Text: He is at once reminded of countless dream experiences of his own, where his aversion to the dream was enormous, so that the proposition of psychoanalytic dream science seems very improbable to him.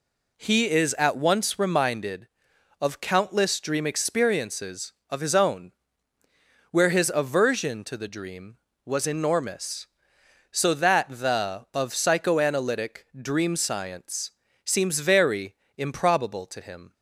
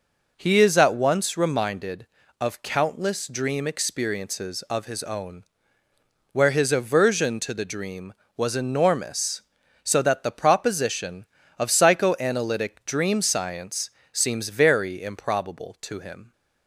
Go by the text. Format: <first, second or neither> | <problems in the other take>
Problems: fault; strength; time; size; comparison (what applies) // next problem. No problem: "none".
second | skips "proposition"; at 11.6 s // pauses between "science" and "seems"; slight; at 14.3 s; 0.32 s long; slight in the second // pauses between "very" and "improbable"; slight; at 15.5 s; 0.22 s long